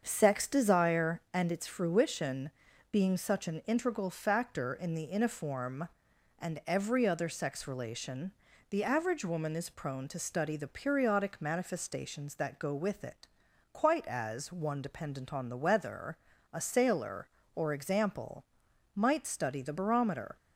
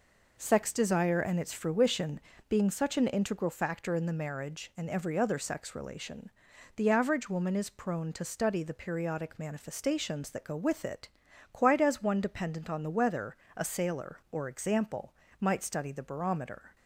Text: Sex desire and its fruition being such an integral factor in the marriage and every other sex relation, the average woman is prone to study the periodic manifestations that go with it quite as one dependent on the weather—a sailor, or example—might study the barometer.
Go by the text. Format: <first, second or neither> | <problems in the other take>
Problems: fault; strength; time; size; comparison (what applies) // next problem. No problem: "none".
second | starts louder than the rest; strong; until 1.0 s; 7 dB // pauses between "fruition" and "being"; at 2.4 s; 0.42 s long; slight in the second // says "iniform" for "marriage"; at 5.0 s // pauses between "it" and "quite"; at 13.2 s; 0.44 s long; also in the second